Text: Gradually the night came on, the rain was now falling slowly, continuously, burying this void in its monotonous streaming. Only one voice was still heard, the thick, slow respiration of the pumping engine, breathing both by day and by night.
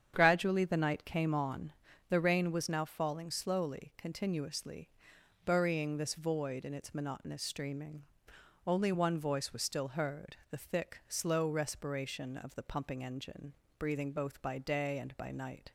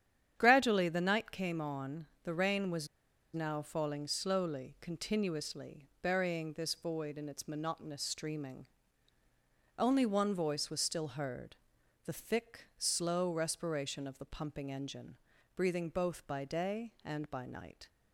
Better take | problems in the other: first | starts louder than the rest; strong; until 1.3 s; 9.5 dB; strong in the first // pauses between "was" and "now"; noticeable; at 2.8 s; 0.48 s long

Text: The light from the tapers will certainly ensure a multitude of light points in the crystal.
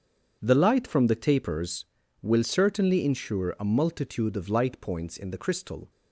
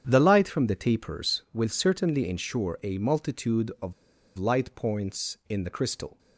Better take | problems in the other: first | starts louder than the rest; strong; until 1.0 s; 8.5 dB; also in the first // pauses between "of" and "light"; at 3.9 s; 0.44 s long

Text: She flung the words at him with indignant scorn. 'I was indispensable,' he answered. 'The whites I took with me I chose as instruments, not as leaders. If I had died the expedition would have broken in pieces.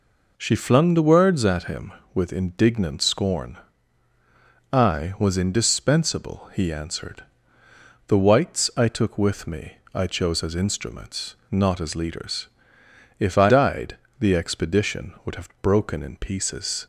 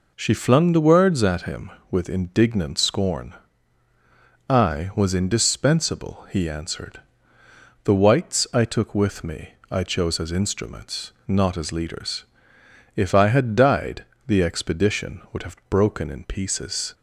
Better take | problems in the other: second | pauses between "me" and "I"; slight; at 9.7 s; 0.16 s long; slight in the second // skips "had"; at 13.4 s // pauses between "died" and "the"; slight; at 13.9 s; 0.24 s long; slight in the second

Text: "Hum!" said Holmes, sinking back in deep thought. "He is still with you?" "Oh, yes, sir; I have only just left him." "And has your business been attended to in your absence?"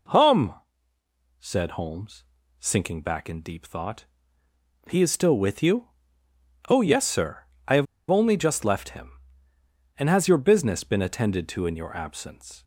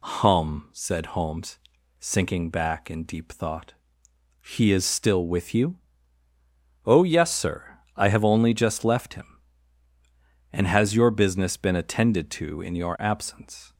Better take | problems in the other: second | pauses between "have" and "only"; slight; at 7.8 s; 0.25 s long

